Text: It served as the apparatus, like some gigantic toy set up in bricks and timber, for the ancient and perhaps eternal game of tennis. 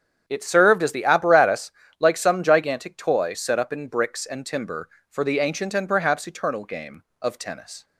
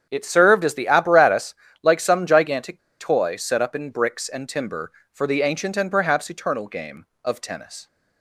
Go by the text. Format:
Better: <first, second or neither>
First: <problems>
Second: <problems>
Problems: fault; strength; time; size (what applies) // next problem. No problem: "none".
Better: first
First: starts louder than the rest; strong; until 1.2 s; 8 dB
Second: starts louder than the rest; strong; until 1.1 s; 8 dB // pauses between "gigantic" and "toy"; slight; at 2.7 s; 0.19 s long